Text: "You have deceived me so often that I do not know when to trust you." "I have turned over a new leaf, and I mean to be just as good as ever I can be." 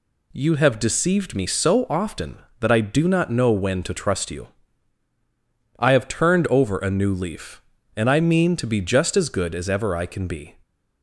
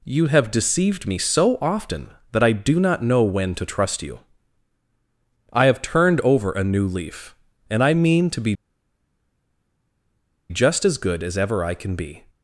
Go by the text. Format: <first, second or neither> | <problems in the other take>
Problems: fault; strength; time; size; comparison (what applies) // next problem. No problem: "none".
first | pauses between "be" and "just"; strong; at 8.5 s; 1.9 s long